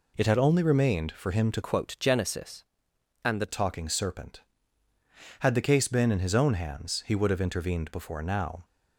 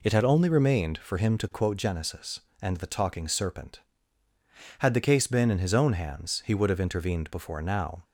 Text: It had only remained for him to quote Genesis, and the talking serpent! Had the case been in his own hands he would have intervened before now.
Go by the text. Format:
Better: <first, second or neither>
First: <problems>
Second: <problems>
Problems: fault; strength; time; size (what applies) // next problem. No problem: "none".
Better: second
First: changes voice from "quote" to "the"; from 1.6 to 3.4 s; 1.8 s long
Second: none